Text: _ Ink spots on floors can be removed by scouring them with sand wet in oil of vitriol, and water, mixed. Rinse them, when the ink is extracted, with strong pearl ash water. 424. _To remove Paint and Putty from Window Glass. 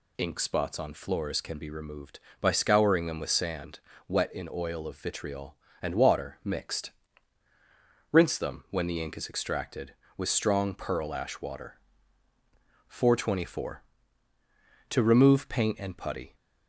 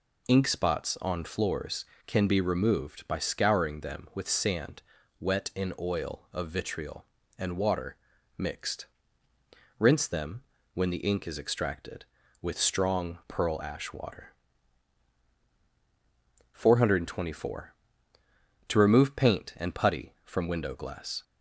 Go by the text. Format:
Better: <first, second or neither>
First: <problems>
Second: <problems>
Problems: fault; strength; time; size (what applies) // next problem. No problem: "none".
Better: second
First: pauses between "sand" and "wet"; slight; at 3.7 s; 0.28 s long // stops before "from Window Glass"; at 16.3 s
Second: pauses between "sand" and "wet"; at 4.8 s; 0.38 s long